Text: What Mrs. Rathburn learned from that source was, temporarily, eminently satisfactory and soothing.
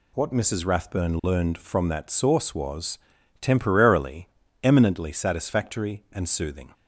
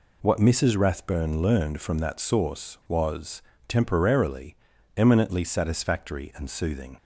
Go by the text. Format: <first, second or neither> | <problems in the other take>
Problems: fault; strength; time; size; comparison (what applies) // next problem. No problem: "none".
neither | none